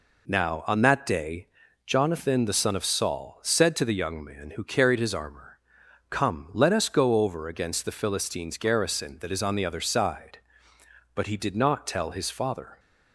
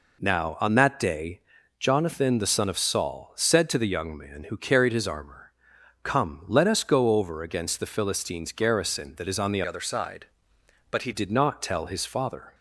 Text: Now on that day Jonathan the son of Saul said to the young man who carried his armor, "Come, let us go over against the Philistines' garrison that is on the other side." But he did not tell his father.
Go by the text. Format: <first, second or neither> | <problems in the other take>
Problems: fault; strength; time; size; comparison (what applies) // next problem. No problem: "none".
first | pauses between "day" and "Jonathan"; at 1.3 s; 0.38 s long; also in the first // changes voice from "other" to "he"; from 9.6 to 11.1 s; 1.5 s long